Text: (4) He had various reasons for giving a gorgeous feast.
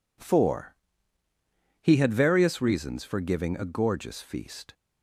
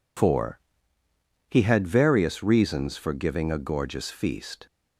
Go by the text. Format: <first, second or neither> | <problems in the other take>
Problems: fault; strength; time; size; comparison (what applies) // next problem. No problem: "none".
neither | none